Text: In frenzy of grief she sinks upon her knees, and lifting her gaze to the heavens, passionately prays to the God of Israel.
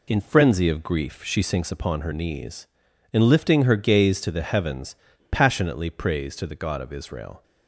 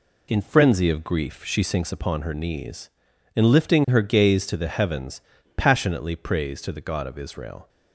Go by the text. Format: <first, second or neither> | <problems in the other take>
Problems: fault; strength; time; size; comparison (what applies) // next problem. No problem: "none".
neither | none